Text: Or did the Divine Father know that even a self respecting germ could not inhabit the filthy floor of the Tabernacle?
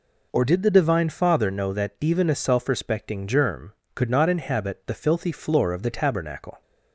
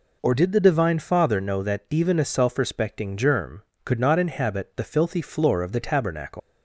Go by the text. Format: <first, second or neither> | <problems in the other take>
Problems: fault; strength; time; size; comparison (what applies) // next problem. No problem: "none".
first | leaves "Tabernacle" unfinished; at 6.3 s; 115 ms